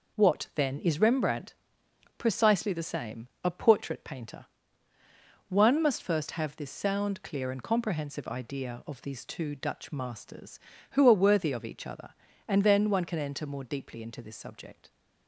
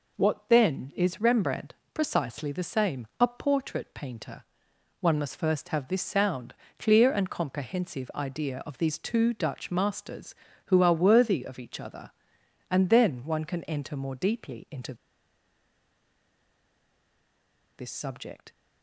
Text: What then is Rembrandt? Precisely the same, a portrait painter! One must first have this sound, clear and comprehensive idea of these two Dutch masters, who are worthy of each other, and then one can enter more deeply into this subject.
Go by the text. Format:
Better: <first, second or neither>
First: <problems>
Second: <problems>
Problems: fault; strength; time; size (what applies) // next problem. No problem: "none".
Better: first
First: none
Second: pauses between "into" and "this"; strong; at 14.9 s; 2.8 s long